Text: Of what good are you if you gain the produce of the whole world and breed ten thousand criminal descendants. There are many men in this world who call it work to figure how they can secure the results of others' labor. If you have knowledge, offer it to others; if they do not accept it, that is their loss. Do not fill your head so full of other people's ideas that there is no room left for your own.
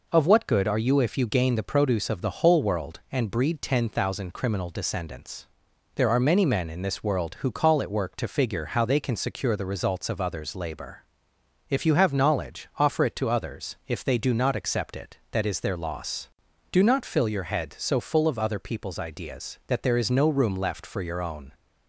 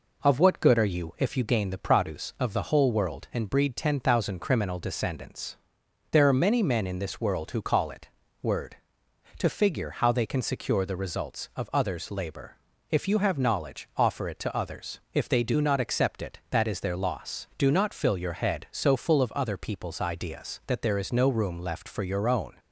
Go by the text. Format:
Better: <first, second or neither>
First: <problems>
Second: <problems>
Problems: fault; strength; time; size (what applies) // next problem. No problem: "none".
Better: first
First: none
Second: says "word" for "work"; at 8.4 s